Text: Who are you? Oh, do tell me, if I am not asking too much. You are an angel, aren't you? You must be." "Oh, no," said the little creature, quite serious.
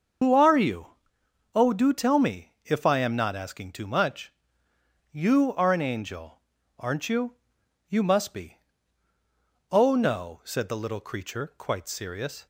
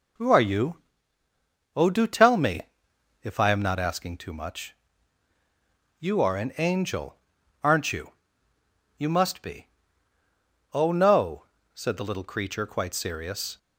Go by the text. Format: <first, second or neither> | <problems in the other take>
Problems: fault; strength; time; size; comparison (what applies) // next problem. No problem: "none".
second | loses the start of "Who"; at 0.2 s; 105 ms // starts louder than the rest; until 1.8 s; 6.5 dB